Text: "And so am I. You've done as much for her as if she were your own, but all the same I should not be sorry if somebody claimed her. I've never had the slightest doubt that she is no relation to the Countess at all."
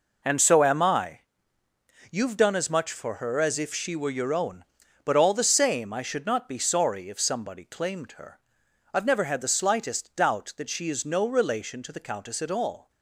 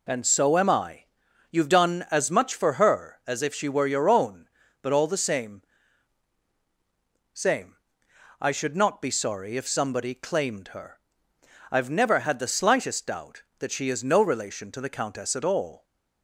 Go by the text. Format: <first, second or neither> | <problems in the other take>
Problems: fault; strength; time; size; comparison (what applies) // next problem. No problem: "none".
first | says "same" twice; at 7.3 s